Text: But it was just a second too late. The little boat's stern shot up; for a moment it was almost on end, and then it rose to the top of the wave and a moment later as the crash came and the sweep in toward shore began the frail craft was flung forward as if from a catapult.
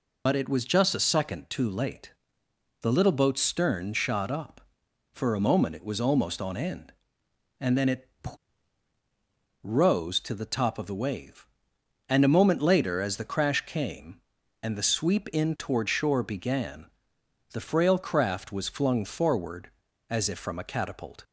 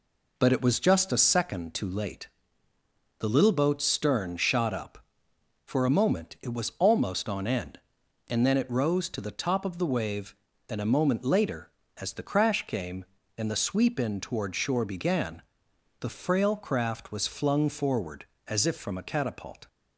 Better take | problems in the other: second | loses the start of "But"; at 0.2 s; 50 ms // pauses between "it" and "rose"; strong; at 8.0 s; 1.5 s long // pauses between "began" and "the"; noticeable; at 16.8 s; 0.68 s long; noticeable in the second

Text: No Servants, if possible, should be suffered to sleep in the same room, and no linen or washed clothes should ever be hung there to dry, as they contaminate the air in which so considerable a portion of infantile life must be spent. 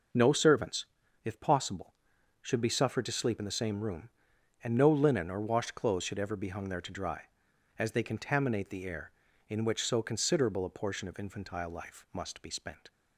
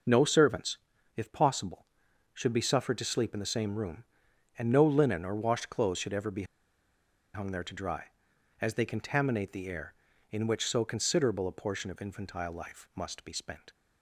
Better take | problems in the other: first | pauses between "be" and "hung"; noticeable; at 6.4 s; 0.90 s long

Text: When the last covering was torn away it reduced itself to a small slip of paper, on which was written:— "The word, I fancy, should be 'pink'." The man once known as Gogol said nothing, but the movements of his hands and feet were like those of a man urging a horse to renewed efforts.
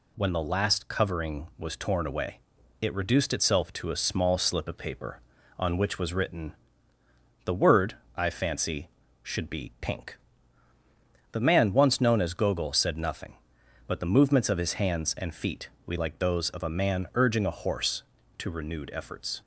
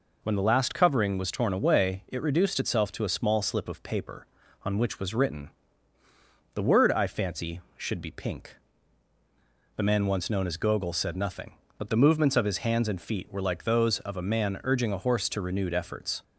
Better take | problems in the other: second | pauses between "away" and "it"; at 2.3 s; 0.42 s long // says "we" for "were"; at 15.8 s

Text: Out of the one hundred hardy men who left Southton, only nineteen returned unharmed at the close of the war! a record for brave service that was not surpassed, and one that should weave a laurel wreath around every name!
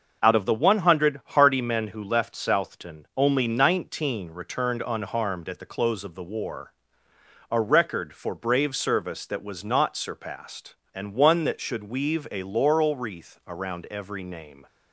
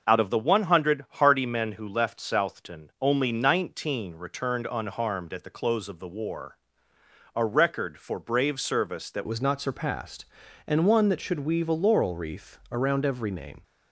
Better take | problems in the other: first | starts louder than the rest; noticeable; until 1.1 s; 6 dB; noticeable in the first // changes voice at "was"; from 9.2 s on; 4.4 s long

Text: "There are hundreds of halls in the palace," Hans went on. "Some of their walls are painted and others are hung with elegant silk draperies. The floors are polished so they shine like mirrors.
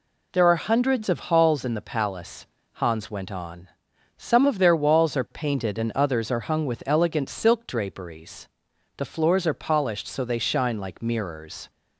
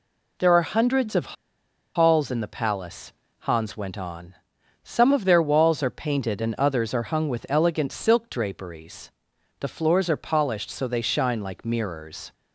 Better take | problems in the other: first | pauses between "of" and "halls"; noticeable; at 1.3 s; 0.62 s long

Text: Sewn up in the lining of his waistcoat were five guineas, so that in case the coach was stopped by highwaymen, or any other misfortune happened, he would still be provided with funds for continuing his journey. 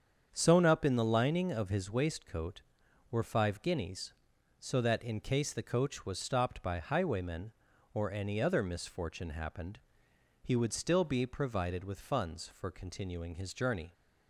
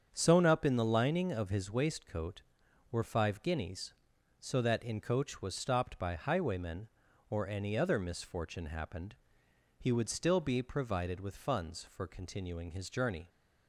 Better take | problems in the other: first | starts louder than the rest; strong; until 1.1 s; 7.5 dB; strong in the first // skips "case the"; at 5.0 s

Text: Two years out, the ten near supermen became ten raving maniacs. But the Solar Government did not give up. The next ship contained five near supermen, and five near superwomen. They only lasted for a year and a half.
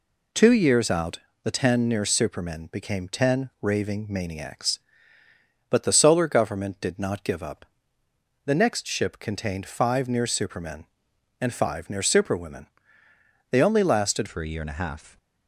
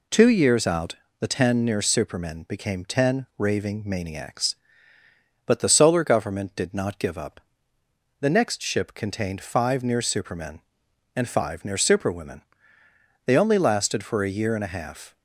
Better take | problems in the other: second | changes voice at "for"; from 14.2 s on; 0.9 s long

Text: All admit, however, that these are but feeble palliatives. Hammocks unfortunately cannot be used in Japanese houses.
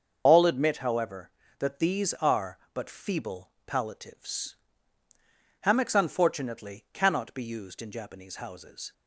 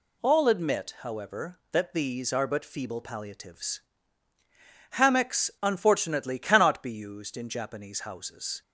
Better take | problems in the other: second | loses the start of "All"; at 0.2 s; 90 ms // starts louder than the rest; until 1.2 s; 6.5 dB // pauses between "feeble" and "palliatives"; slight; at 3.5 s; 0.16 s long

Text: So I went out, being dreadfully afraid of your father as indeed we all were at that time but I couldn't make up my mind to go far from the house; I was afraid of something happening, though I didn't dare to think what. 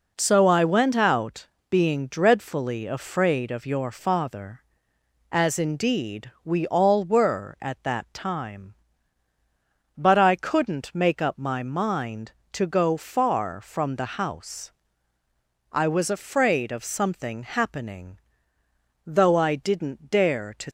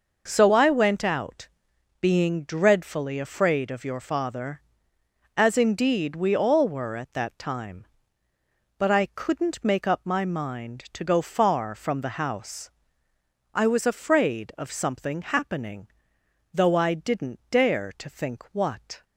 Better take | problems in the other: second | stops before "think what"; at 20.6 s

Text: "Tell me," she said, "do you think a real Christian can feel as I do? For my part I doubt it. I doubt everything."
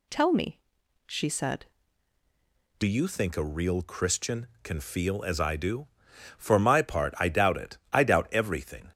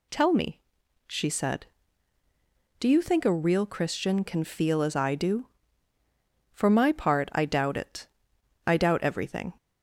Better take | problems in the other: second | changes voice at "you"; from 2.8 s on; 6.1 s long

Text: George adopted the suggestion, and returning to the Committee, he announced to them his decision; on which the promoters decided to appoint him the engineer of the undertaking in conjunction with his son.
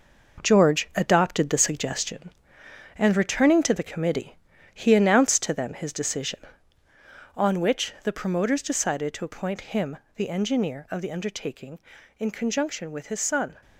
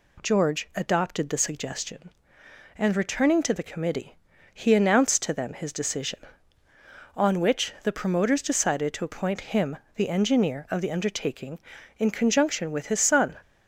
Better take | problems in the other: second | gets quieter; throughout; 6.5 dB // pauses between "him" and "the"; slight; at 9.9 s; 0.18 s long; slight in the second

